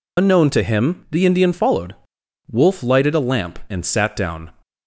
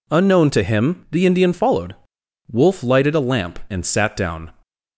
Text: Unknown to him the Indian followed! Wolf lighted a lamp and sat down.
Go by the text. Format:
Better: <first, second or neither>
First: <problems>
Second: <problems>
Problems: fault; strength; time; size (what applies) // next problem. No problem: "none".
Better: second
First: loses the start of "Unknown"; at 0.1 s; 85 ms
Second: none